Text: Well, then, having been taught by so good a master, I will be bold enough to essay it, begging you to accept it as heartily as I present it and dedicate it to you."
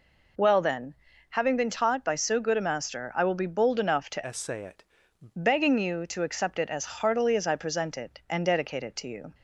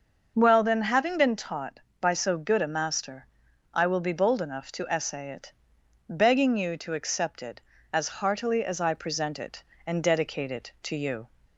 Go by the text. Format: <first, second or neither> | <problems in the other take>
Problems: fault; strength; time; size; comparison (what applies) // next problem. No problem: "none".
second | changes voice from "essay" to "it"; from 4.2 to 4.8 s; 0.6 s long